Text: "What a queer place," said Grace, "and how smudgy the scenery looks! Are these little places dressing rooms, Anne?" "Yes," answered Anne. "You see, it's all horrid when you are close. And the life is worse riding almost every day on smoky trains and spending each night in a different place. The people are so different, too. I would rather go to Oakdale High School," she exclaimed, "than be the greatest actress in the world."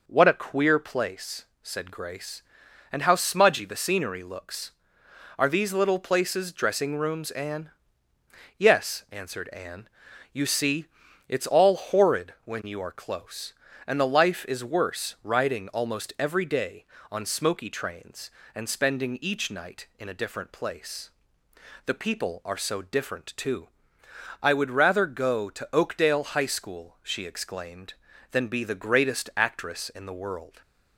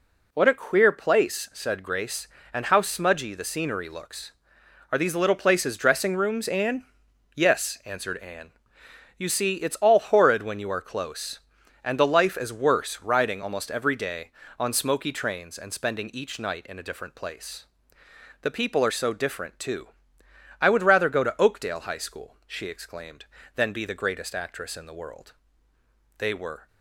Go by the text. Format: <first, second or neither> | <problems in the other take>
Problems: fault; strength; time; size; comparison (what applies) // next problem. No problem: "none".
first | goes on to say "They were"; from 26.1 s on; 0.50 s long